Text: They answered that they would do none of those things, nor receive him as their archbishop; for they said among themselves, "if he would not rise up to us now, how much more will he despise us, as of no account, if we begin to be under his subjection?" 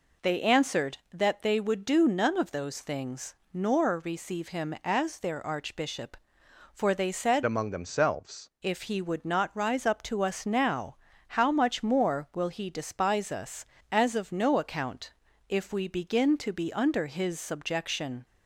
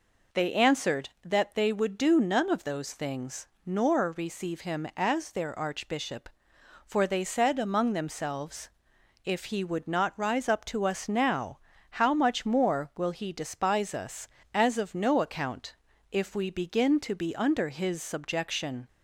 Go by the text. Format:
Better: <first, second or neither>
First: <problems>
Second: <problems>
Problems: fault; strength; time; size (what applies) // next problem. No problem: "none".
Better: second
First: changes voice from "among" to "themselves"; from 7.4 to 8.4 s; 1.0 s long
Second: none